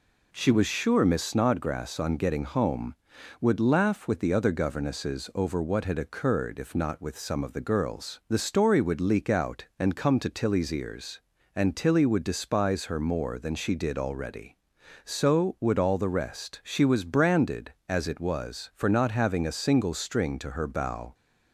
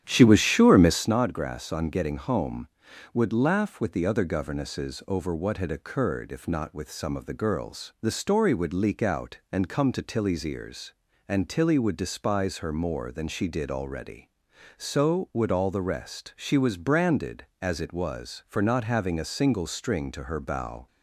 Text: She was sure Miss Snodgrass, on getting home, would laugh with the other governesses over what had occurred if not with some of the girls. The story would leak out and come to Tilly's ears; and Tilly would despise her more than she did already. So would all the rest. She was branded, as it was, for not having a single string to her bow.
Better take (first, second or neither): first